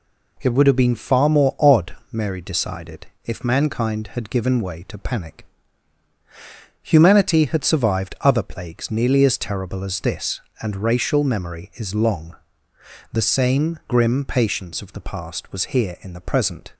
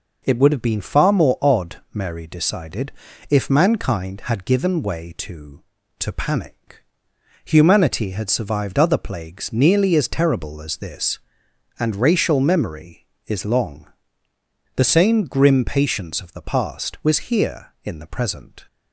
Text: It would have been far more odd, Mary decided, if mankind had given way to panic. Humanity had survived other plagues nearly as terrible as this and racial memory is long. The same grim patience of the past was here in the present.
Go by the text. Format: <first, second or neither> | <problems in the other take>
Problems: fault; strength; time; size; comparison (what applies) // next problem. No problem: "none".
first | says "to" twice; at 5.9 s